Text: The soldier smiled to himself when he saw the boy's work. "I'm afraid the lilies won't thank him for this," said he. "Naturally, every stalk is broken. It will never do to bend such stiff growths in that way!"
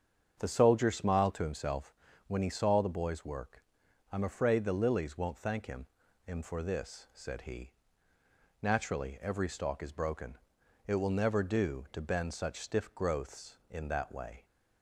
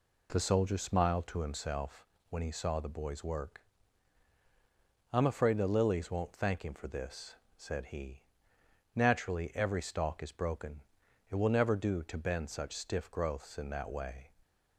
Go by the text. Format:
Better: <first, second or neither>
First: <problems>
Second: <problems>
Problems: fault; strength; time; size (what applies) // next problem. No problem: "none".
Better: second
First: starts louder than the rest; strong; until 1.3 s; 7.5 dB // pauses between "himself" and "when"; slight; at 1.9 s; 0.36 s long // says "him" twice; at 6.2 s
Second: pauses between "himself" and "when"; slight; at 2.0 s; 0.24 s long